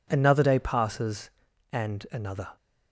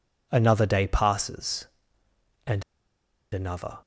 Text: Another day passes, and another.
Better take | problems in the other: first | pauses between "and" and "another"; noticeable; at 2.6 s; 0.69 s long

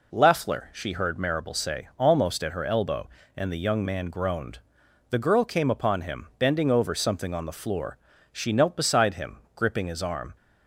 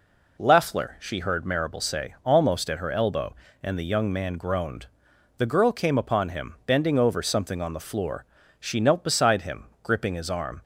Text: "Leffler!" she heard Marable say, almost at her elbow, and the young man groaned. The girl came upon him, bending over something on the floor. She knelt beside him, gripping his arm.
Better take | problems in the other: neither | none

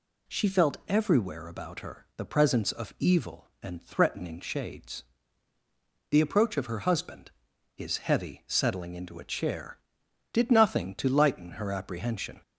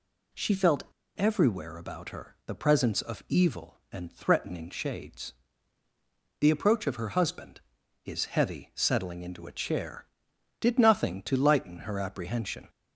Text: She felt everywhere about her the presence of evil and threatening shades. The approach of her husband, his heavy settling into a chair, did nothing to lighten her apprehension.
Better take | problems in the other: first | pauses between "felt" and "everywhere"; slight; at 0.8 s; 0.33 s long

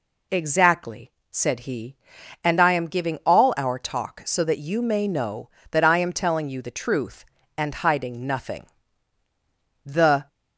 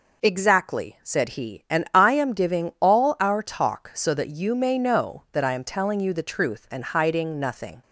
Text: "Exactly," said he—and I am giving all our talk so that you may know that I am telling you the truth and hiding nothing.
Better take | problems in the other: second | goes on to say "The"; slight; from 9.8 s on; 0.44 s long

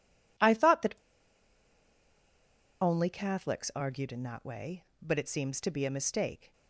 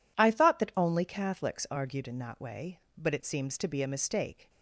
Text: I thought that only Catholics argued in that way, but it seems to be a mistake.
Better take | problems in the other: second | pauses between "that" and "only"; strong; at 0.9 s; 1.8 s long

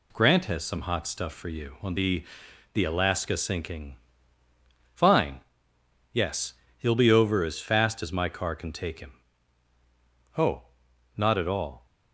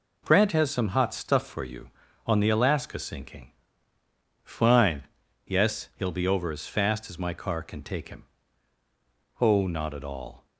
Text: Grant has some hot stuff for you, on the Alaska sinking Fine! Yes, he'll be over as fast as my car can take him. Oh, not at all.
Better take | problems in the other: second | says "the" twice; at 2.7 s // pauses between "sinking" and "Fine"; noticeable; at 3.9 s; 0.96 s long; noticeable in the second

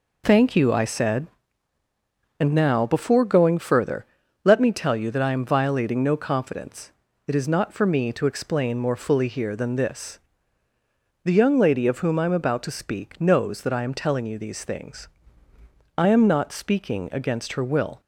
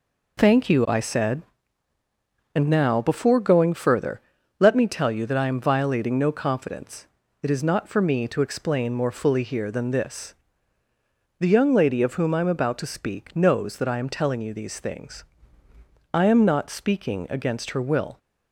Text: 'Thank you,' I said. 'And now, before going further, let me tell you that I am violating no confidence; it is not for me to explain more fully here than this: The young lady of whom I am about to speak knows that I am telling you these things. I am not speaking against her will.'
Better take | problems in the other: neither | none

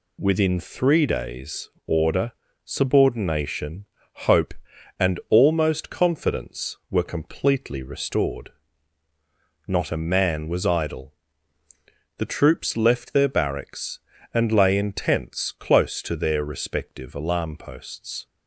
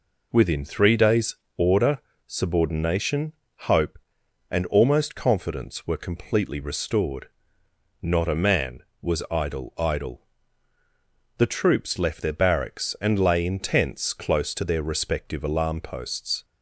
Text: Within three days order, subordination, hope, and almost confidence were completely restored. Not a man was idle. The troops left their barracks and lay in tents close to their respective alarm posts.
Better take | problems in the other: first | pauses between "days" and "order"; slight; at 1.3 s; 0.22 s long; slight in the first // says "idle" twice; at 9.7 s

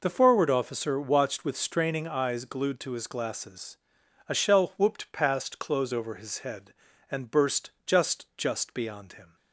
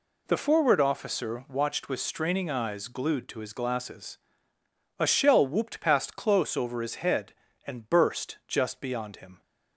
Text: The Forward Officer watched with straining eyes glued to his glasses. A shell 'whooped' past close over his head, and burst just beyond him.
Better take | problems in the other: second | pauses between "burst" and "just"; slight; at 7.6 s; 0.16 s long // says "just" twice; at 8.3 s

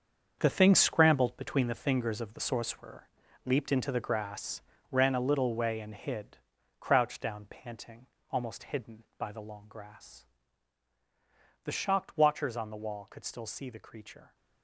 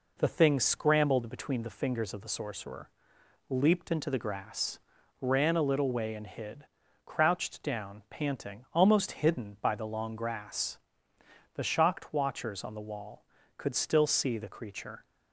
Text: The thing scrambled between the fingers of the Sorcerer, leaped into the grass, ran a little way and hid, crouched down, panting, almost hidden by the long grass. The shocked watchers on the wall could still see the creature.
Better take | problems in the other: second | gets quieter; strong; throughout; 11.5 dB

